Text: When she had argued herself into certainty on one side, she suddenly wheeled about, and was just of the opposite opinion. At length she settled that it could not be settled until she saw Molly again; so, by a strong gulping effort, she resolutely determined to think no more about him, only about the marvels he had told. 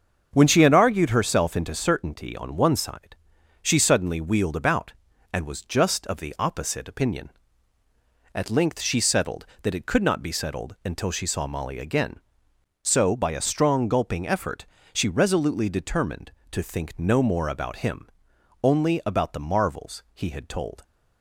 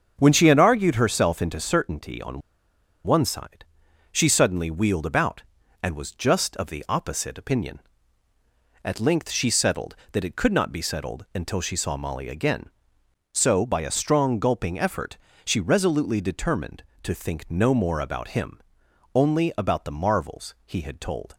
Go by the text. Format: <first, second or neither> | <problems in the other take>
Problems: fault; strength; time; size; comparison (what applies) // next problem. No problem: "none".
first | starts louder than the rest; until 1.2 s; 7 dB; also in the first // pauses between "on" and "one"; noticeable; at 2.4 s; 0.64 s long